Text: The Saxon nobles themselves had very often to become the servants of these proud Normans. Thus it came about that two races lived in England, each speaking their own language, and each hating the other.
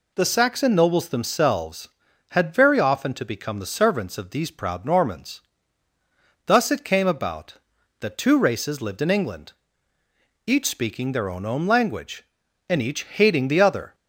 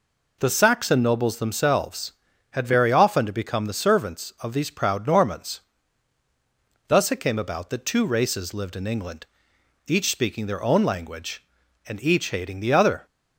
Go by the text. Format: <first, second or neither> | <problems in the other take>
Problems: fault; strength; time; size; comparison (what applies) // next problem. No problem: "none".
second | says "own" twice; at 11.4 s